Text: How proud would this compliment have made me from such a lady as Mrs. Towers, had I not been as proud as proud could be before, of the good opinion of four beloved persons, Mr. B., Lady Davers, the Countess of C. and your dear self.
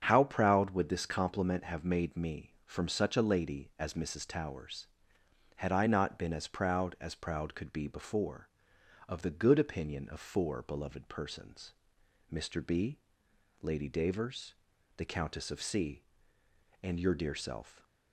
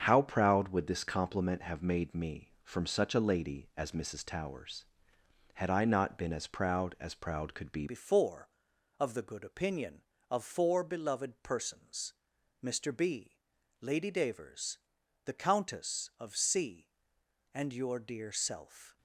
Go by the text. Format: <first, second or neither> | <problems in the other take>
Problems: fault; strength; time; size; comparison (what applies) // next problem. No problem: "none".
first | starts louder than the rest; strong; until 1.0 s; 7 dB; strong in the first // changes voice at "before"; from 7.8 s on; 11.1 s long